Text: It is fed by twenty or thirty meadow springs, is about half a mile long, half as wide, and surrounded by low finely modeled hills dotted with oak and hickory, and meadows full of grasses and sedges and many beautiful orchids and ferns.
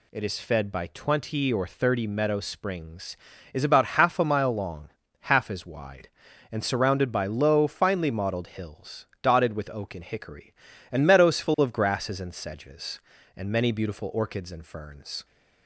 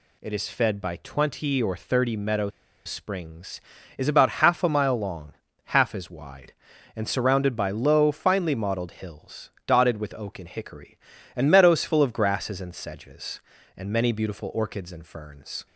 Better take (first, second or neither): first